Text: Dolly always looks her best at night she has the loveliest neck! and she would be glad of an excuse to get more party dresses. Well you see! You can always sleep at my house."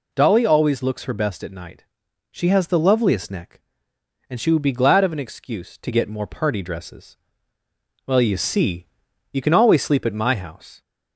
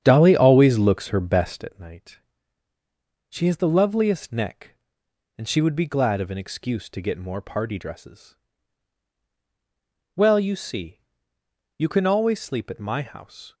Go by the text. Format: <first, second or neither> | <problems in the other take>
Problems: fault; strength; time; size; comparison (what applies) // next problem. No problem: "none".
first | starts louder than the rest; strong; until 1.7 s; 9 dB // pauses between "night" and "she"; at 2.1 s; 1.1 s long; noticeable in the first